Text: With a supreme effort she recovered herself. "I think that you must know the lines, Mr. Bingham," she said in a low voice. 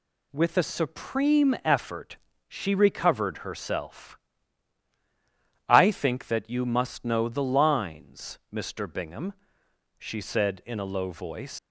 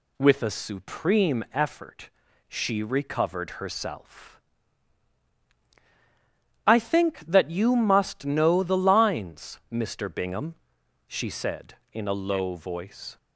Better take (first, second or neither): second